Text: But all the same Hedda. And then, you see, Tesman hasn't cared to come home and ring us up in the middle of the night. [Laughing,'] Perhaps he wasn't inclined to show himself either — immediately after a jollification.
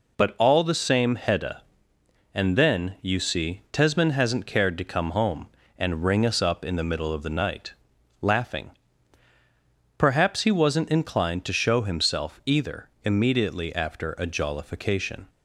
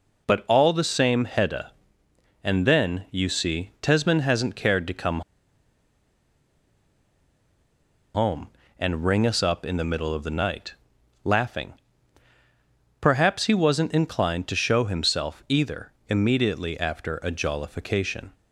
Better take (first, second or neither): first